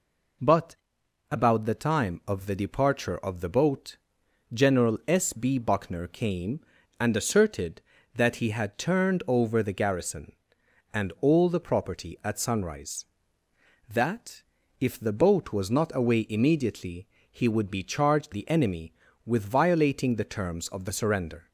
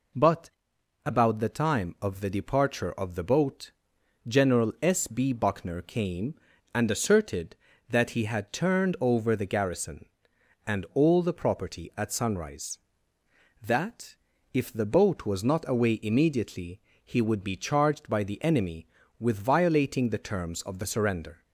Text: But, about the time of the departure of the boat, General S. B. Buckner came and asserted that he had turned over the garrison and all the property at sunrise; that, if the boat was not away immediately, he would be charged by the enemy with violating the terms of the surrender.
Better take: second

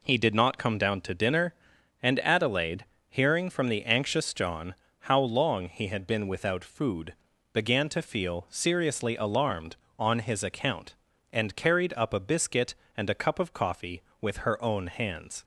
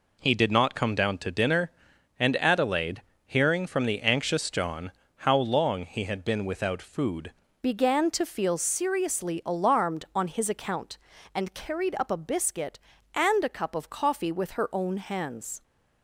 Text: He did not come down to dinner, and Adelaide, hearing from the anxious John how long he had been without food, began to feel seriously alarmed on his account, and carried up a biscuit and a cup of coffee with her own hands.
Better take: first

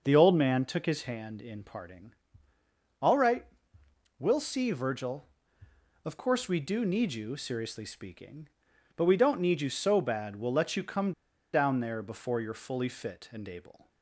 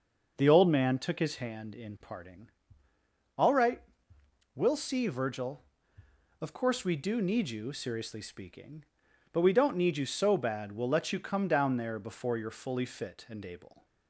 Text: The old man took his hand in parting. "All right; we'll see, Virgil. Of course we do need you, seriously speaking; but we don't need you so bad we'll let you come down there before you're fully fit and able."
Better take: second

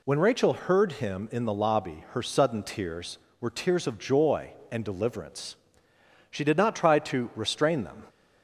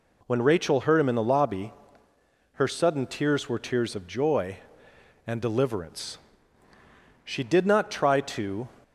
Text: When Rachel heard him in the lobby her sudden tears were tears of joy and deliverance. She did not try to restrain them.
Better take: first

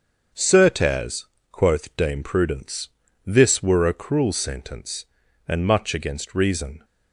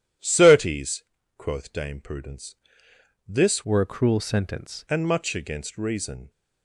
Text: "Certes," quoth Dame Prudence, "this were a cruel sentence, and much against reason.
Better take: first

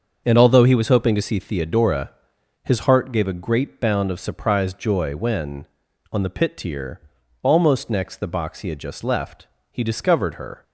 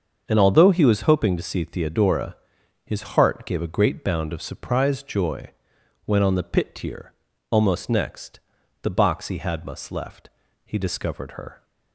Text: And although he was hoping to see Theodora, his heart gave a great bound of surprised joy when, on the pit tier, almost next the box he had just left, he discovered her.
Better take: first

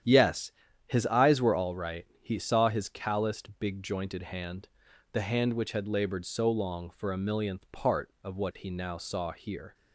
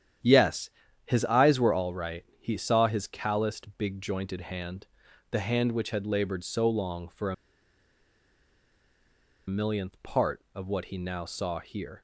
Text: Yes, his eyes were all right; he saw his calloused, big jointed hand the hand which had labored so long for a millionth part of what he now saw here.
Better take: first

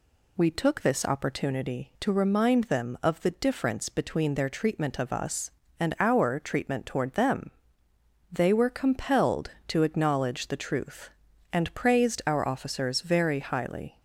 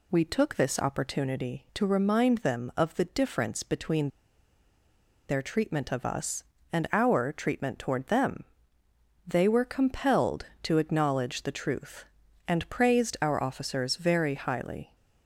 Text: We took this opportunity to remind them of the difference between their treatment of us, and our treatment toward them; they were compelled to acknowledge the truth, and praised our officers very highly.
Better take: first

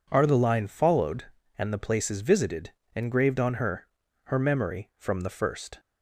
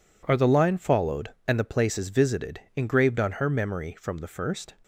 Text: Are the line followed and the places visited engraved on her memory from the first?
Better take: second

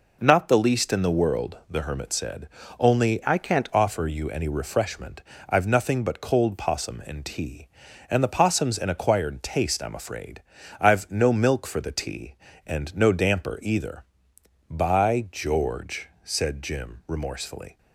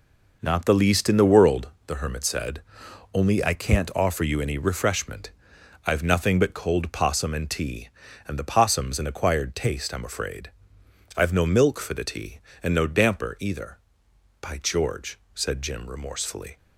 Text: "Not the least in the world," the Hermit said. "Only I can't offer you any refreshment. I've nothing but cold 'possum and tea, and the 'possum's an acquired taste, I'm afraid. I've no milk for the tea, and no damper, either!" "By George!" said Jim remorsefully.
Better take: second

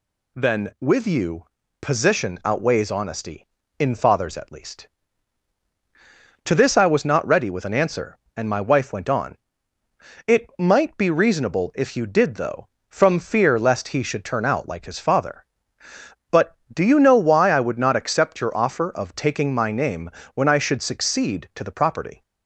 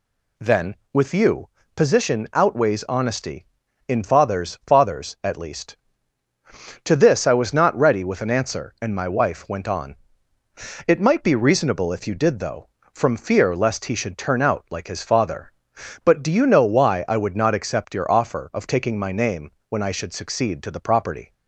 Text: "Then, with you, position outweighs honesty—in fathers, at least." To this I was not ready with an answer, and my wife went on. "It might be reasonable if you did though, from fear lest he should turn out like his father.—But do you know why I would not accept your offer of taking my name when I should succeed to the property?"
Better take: first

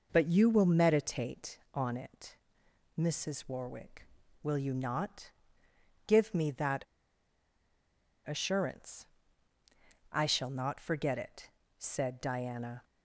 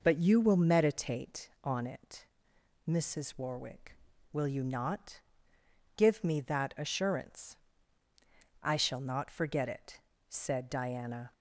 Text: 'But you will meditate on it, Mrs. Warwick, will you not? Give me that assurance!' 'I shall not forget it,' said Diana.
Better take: second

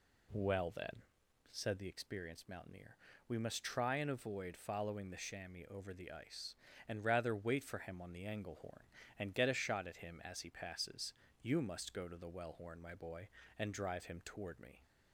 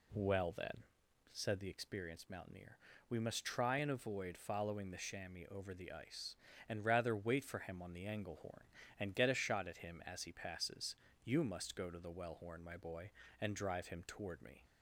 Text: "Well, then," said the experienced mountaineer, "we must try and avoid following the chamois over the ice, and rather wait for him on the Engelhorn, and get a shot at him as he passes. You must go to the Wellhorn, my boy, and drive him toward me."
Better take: neither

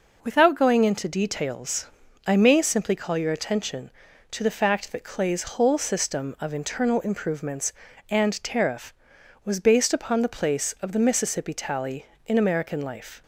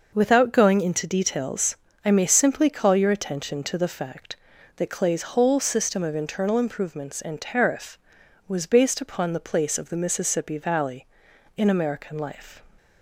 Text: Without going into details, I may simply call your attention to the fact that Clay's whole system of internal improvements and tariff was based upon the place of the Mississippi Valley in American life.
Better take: second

